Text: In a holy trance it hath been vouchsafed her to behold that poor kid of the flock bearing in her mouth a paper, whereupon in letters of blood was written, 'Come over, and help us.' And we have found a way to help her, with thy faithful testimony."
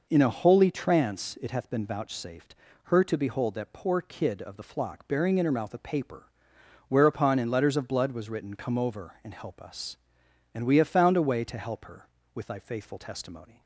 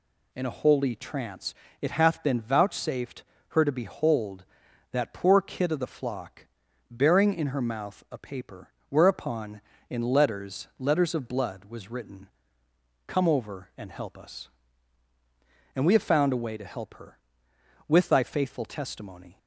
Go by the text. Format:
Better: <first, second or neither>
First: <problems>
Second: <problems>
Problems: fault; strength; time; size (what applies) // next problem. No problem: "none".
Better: first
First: pauses between "vouchsafed" and "her"; slight; at 2.5 s; 0.28 s long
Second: pauses between "trance" and "it"; slight; at 1.5 s; 0.26 s long // pauses between "vouchsafed" and "her"; slight; at 3.2 s; 0.26 s long // pauses between "flock" and "bearing"; at 6.4 s; 0.44 s long // says "letters" twice; at 10.7 s